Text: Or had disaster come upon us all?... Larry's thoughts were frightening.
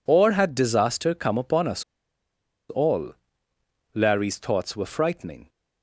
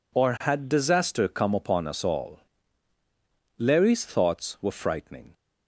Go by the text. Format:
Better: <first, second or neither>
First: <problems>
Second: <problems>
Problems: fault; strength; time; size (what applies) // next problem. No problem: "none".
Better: second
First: pauses between "us" and "all"; noticeable; at 1.8 s; 0.86 s long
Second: none